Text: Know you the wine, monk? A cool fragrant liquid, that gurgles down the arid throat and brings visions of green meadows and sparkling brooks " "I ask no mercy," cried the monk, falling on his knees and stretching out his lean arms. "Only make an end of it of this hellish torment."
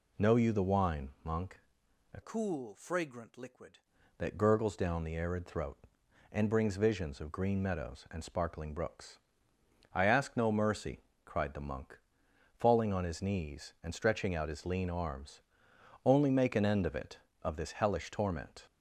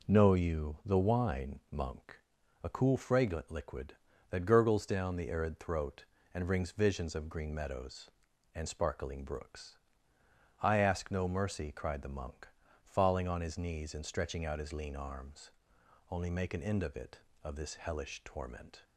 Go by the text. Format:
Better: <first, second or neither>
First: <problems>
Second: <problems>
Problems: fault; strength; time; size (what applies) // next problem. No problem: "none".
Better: second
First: changes voice from "cool" to "liquid"; from 2.2 to 3.7 s; 1.5 s long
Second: none